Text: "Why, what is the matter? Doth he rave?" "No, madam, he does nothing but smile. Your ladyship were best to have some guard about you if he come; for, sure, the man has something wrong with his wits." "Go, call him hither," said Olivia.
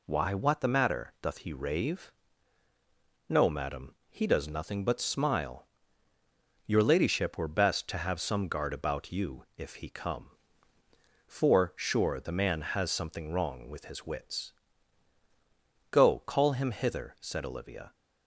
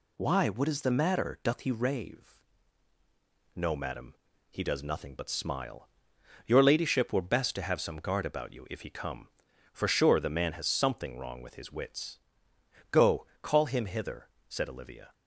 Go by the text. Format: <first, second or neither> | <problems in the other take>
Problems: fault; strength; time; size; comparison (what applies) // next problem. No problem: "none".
second | skips "is"; at 0.6 s